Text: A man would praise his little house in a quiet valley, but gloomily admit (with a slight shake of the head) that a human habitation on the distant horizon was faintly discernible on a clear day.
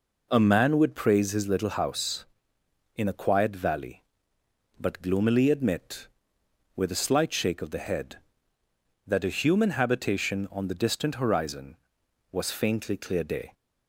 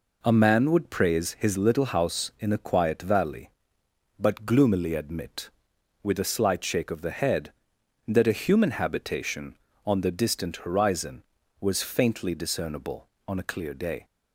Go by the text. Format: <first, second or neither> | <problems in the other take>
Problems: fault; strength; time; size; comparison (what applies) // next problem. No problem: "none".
second | skips "discernible on a"; at 12.9 s